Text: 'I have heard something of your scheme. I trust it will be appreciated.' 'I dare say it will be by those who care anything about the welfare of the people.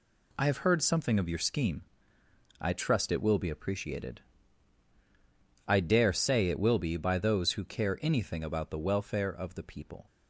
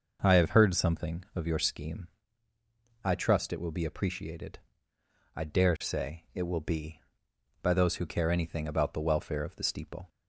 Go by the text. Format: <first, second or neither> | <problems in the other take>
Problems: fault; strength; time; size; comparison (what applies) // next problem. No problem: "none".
first | says "steeple" for "people"; at 9.6 s